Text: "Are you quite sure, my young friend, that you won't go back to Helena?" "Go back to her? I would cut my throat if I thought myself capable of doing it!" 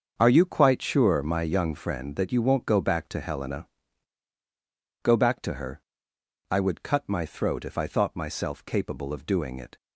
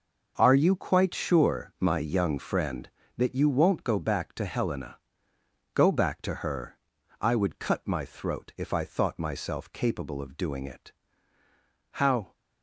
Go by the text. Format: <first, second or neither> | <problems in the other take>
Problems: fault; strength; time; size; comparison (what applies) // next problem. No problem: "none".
first | starts louder than the rest; noticeable; until 1.3 s; 6 dB; also in the first // goes on to say "How"; slight; from 11.9 s on; 0.40 s long